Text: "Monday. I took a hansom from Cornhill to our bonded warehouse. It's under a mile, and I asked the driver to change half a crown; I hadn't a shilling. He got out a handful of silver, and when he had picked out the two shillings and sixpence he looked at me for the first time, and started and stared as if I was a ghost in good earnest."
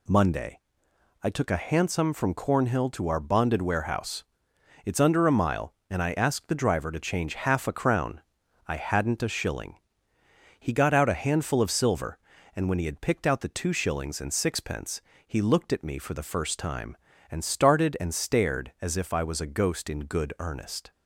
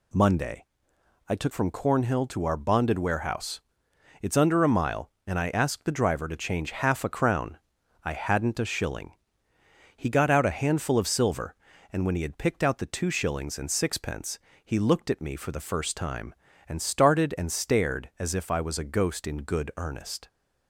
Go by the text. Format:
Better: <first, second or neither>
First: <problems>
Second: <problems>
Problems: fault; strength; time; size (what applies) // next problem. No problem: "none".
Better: first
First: pauses between "sixpence" and "he"; slight; at 15.0 s; 0.26 s long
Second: skips "a hansom"; at 1.5 s // pauses between "sixpence" and "he"; slight; at 14.3 s; 0.26 s long